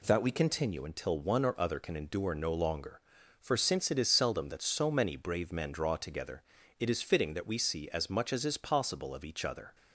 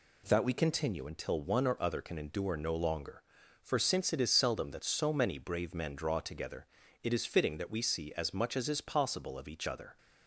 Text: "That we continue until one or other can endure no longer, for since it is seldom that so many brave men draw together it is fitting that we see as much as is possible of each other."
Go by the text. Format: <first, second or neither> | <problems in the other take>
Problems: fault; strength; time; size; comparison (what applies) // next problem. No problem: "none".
neither | pauses between "together" and "it"; the same in both